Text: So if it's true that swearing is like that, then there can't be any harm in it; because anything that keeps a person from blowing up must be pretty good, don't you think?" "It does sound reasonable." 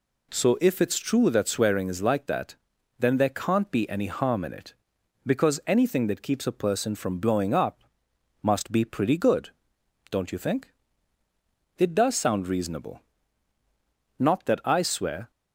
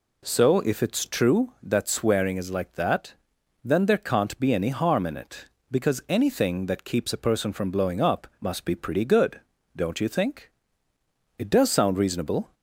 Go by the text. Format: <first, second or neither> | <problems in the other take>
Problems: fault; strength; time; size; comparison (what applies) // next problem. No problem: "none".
second | pauses between "up" and "must"; noticeable; at 7.8 s; 0.60 s long // goes on to say "Not that I swear"; noticeable; from 14.1 s on; 1.1 s long